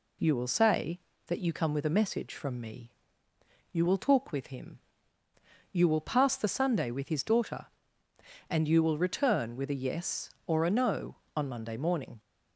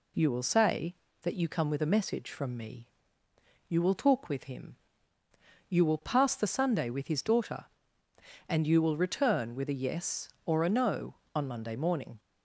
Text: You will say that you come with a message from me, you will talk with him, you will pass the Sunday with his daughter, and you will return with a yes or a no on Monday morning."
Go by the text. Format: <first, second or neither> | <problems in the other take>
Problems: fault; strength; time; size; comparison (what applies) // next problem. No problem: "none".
neither | none